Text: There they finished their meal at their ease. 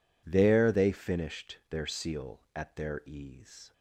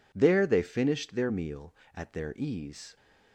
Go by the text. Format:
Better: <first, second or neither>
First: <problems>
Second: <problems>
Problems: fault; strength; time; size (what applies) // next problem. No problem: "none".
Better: second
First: says "seal" for "meal"; at 1.8 s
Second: none